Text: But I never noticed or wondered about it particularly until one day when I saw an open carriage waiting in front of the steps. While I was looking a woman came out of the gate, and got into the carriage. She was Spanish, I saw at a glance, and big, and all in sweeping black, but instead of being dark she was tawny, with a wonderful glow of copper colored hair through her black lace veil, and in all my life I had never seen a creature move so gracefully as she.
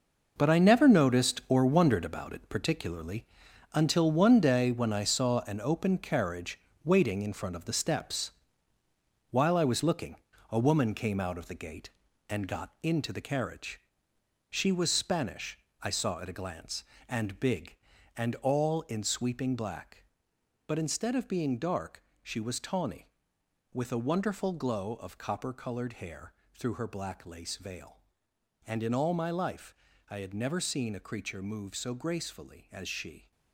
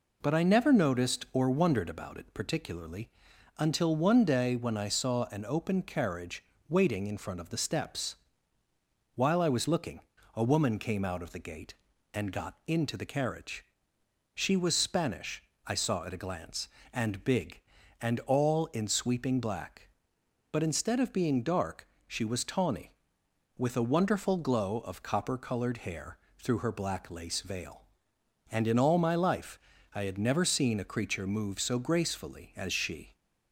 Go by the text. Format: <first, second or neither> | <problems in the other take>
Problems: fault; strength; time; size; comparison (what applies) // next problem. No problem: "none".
second | gets quieter; strong; throughout; 10.5 dB // pauses between "particularly" and "until"; noticeable; at 3.2 s; 0.48 s long; noticeable in the second // pauses between "carriage" and "waiting"; slight; at 6.5 s; 0.26 s long; slight in the second // pauses between "looking" and "a"; slight; at 10.1 s; 0.34 s long; slight in the second // pauses between "dark" and "she"; slight; at 22.0 s; 0.22 s long; slight in the second // pauses between "hair" and "through"; slight; at 26.3 s; 0.20 s long; slight in the second // pauses between "life" and "I"; slight; at 29.7 s; 0.34 s long; slight in the second